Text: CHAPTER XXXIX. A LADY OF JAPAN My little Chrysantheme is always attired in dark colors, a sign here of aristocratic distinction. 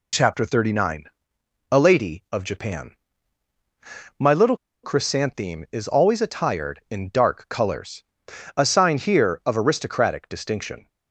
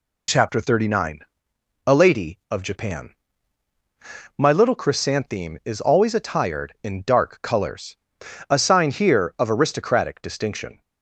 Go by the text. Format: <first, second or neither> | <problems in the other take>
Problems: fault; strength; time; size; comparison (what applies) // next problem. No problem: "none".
second | pauses between "JAPAN" and "My"; strong; at 2.9 s; 1.2 s long; strong in the second // pauses between "little" and "Chrysantheme"; slight; at 4.5 s; 0.27 s long